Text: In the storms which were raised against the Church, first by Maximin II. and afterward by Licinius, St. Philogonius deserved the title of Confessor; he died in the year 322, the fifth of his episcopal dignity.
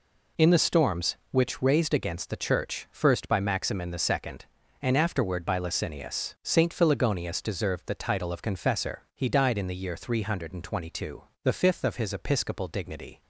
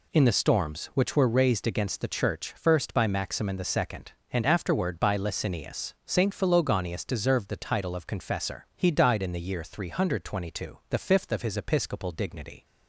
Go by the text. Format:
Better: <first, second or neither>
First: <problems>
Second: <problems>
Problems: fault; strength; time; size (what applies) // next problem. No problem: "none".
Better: second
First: skips "were"; at 1.6 s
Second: none